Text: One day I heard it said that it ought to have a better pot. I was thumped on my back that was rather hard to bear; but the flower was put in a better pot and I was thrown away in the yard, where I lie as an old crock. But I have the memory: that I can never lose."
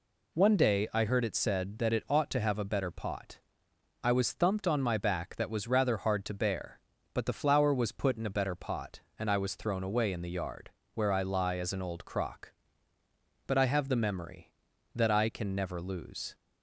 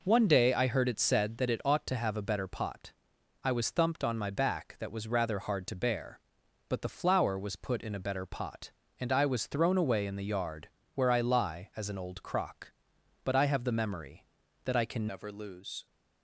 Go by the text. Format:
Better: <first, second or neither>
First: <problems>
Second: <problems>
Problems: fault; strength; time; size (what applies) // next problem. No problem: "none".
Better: first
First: none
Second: changes voice at "never"; from 15.0 s on; 0.8 s long